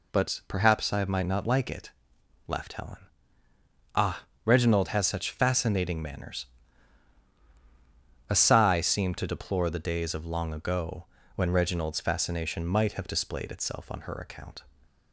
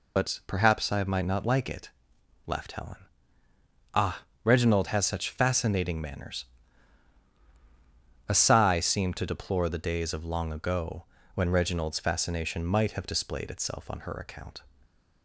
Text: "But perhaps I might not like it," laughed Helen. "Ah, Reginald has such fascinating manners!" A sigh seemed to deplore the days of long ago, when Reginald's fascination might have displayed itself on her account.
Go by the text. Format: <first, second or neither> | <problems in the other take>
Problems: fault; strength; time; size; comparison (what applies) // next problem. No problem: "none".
first | loses the start of "But"; at 0.1 s; 50 ms